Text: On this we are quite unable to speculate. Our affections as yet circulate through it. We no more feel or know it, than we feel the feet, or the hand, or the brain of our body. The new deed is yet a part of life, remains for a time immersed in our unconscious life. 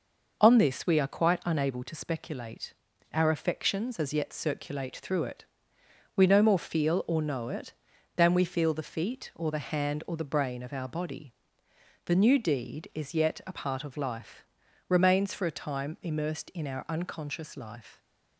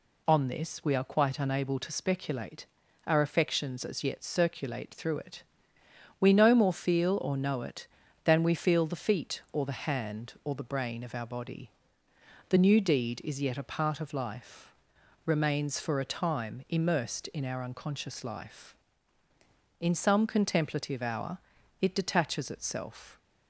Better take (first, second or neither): first